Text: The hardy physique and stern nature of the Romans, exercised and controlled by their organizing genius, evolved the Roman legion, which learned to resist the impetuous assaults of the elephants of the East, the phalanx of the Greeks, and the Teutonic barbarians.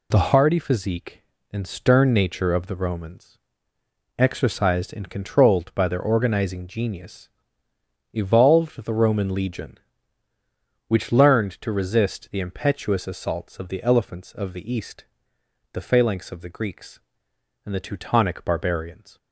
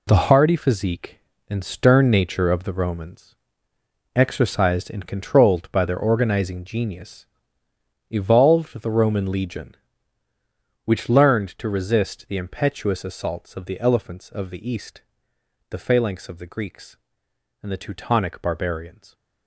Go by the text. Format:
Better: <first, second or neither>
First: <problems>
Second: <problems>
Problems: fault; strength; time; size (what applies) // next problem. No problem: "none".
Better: first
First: none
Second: gets quieter; strong; throughout; 9.5 dB